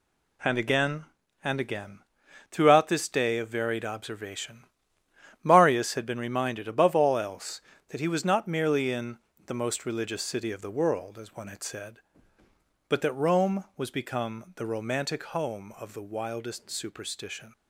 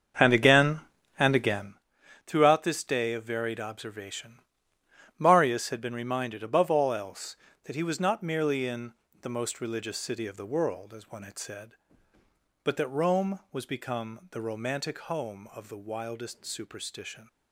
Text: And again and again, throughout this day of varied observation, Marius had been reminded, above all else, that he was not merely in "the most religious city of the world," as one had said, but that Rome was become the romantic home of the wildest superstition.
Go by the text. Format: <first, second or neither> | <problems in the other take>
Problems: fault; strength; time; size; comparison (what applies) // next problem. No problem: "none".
first | starts louder than the rest; strong; until 1.8 s; 7 dB // pauses between "in" and "the"; slight; at 8.9 s; 0.26 s long; slight in the first